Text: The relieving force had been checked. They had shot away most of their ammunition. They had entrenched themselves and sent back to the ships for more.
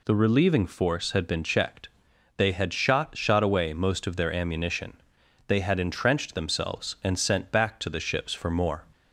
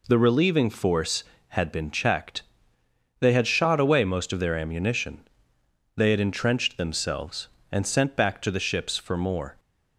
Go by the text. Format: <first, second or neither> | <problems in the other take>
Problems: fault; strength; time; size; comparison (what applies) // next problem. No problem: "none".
second | says "shot" twice; at 3.1 s